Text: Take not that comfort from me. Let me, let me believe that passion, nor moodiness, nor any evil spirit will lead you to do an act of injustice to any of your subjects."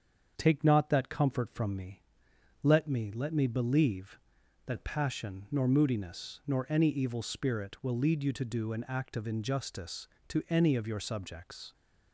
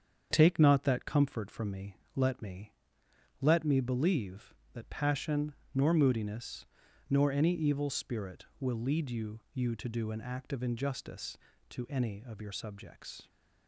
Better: first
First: starts louder than the rest; strong; until 1.3 s; 7 dB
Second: starts louder than the rest; strong; until 1.3 s; 7.5 dB // says "you" twice; at 9.5 s

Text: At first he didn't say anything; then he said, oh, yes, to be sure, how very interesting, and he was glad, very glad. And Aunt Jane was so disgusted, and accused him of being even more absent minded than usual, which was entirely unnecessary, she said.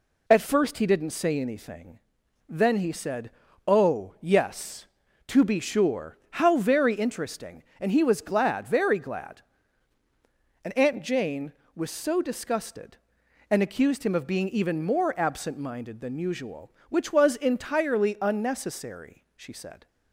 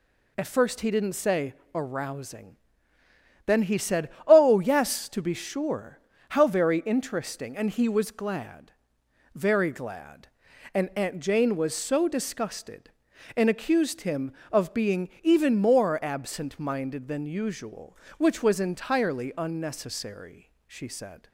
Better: first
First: none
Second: says "arousing" for "anything"; at 1.7 s

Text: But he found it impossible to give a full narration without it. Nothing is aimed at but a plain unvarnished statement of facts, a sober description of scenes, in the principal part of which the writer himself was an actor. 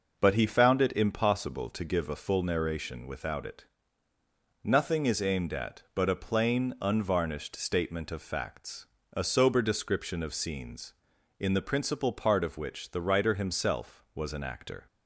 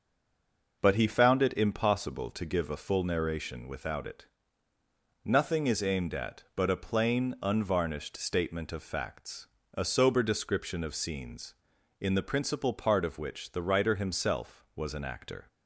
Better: first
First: none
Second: stays silent before the first word; slight; until 0.8 s; 0.8 s long

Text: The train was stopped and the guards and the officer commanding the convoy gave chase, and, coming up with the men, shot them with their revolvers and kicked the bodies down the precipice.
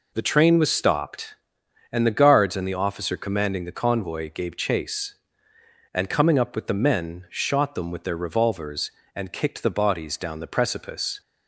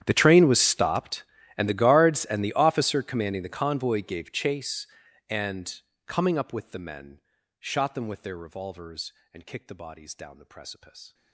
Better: first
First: none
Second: gets quieter; strong; throughout; 25 dB

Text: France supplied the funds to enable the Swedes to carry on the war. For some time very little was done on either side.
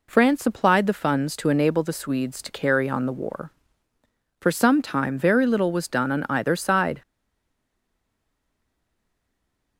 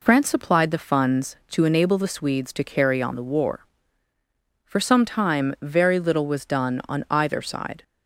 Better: second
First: stays silent after the last word; strong; from 7.0 s on; 2.7 s long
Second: none

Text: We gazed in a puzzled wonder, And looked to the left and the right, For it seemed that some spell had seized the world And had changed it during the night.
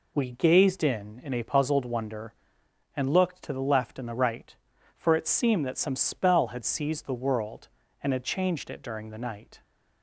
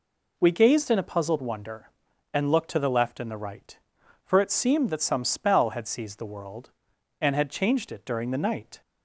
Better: second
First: says "in" twice; at 1.2 s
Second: none

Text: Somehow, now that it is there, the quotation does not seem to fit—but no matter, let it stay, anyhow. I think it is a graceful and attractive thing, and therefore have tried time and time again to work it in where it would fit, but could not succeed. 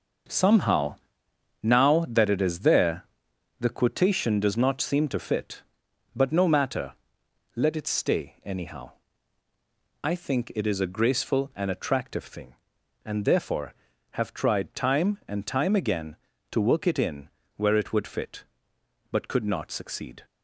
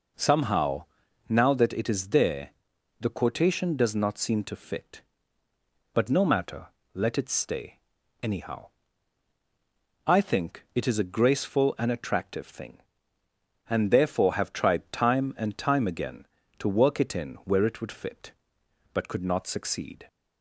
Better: second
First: gets quieter; strong; throughout; 9 dB // pauses between "in" and "where"; slight; at 17.2 s; 0.26 s long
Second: none

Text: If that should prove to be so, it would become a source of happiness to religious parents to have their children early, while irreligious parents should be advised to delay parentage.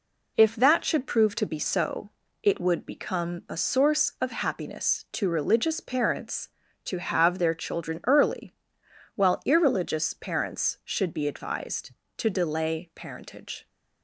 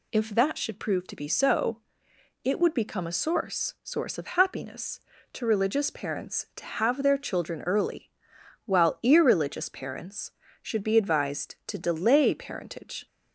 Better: first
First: none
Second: says "source" twice; at 3.8 s

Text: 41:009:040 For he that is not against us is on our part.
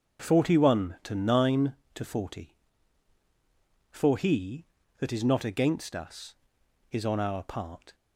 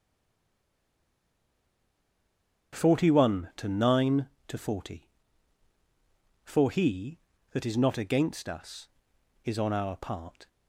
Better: first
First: starts louder than the rest; until 1.2 s; 6 dB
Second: stays silent before the first word; strong; until 2.7 s; 2.7 s long // starts louder than the rest; until 3.8 s; 6 dB

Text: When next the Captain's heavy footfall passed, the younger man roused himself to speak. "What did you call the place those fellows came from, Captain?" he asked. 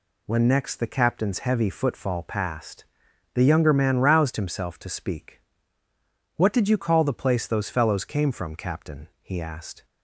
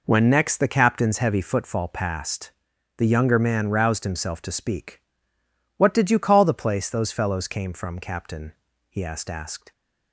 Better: first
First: none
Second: says "asked" twice; at 9.3 s

